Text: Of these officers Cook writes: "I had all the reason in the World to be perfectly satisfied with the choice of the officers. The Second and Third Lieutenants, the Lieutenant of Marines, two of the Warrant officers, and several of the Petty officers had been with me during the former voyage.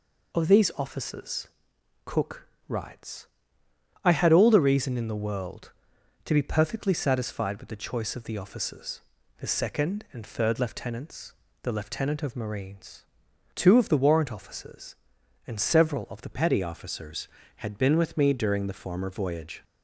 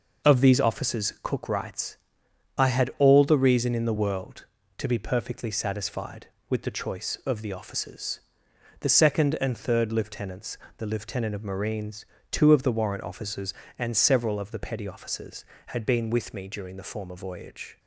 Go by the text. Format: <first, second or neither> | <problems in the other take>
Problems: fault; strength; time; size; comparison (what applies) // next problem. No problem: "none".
second | pauses between "officers" and "Cook"; noticeable; at 1.4 s; 0.60 s long // pauses between "Cook" and "writes"; slight; at 2.4 s; 0.20 s long // changes voice at "Petty"; from 16.3 s on; 3.3 s long